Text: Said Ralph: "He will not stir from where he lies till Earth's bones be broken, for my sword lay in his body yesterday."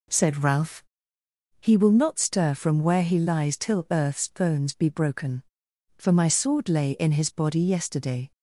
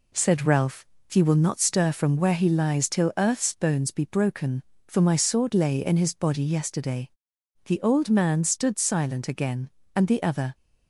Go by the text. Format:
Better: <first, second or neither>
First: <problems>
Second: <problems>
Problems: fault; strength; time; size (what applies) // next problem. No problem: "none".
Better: first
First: none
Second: goes on to say "The old man stood silent again and the other"; strong; from 7.6 s on; 2.9 s long